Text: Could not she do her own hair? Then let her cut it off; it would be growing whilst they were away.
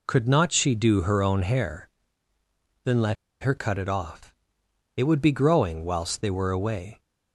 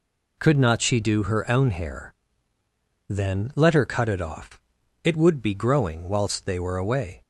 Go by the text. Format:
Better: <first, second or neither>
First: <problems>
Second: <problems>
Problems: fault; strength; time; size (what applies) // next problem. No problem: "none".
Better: second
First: pauses between "let" and "her"; slight; at 3.1 s; 0.27 s long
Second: none